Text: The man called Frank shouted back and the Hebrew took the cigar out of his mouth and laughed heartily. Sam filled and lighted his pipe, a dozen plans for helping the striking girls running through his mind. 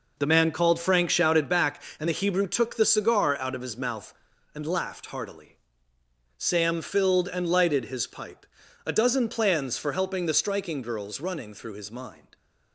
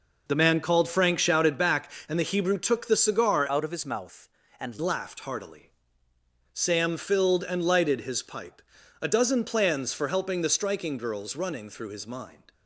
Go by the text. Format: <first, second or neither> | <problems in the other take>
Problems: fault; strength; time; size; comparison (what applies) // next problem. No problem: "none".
first | changes voice from "out" to "and"; from 3.4 to 4.7 s; 1.3 s long